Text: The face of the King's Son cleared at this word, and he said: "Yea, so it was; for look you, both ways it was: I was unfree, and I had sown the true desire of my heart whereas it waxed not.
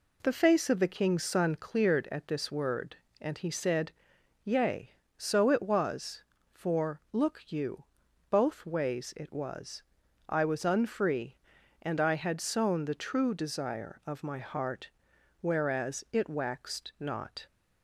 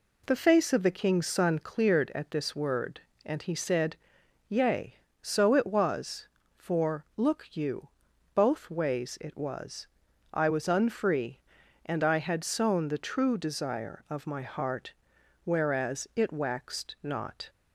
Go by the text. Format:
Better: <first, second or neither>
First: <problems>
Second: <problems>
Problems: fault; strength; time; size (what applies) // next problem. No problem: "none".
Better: neither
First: pauses between "heart" and "whereas"; noticeable; at 14.9 s; 0.50 s long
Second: pauses between "heart" and "whereas"; noticeable; at 14.9 s; 0.50 s long